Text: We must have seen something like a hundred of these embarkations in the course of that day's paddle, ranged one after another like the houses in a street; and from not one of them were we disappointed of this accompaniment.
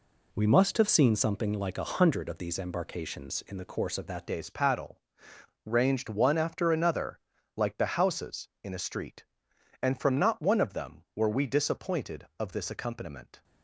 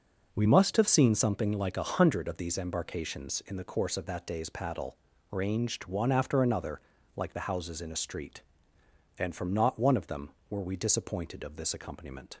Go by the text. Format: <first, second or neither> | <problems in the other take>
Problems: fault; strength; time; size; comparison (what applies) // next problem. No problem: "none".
second | changes voice at "day's"; from 4.2 s on; 9.2 s long // pauses between "another" and "like"; slight; at 7.1 s; 0.36 s long; slight in the second